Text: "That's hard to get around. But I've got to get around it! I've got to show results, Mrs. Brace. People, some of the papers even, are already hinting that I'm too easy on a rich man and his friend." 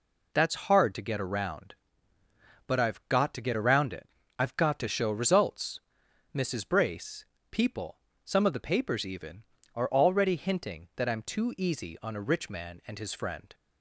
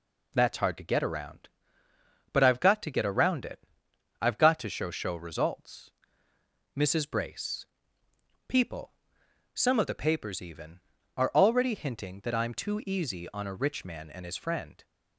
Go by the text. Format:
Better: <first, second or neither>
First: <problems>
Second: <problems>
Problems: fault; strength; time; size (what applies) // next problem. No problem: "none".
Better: first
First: none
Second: says "show" twice; at 4.8 s